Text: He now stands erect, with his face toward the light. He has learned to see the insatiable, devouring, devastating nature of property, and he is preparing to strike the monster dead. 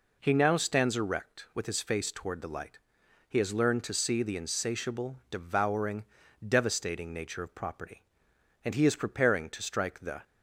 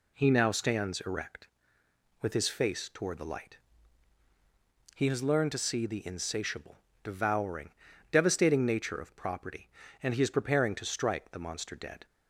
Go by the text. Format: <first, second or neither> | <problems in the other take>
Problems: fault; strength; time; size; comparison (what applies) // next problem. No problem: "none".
second | stops before "monster dead"; at 10.2 s